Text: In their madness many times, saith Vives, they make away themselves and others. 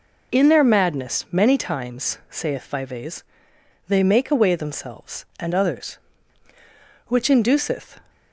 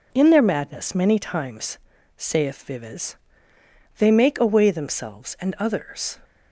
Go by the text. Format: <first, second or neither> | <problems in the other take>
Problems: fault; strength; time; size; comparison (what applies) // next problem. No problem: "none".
second | goes on to say "Which induceth"; noticeable; from 7.0 s on; 0.92 s long